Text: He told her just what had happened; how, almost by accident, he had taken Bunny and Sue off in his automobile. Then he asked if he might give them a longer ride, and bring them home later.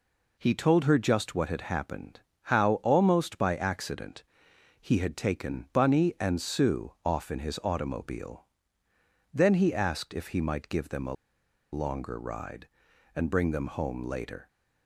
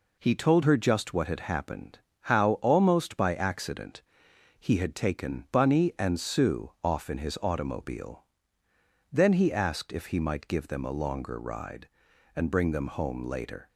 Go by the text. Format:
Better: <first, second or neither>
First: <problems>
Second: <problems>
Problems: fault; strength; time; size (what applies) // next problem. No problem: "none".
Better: second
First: pauses between "a" and "longer"; noticeable; at 11.1 s; 0.58 s long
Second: none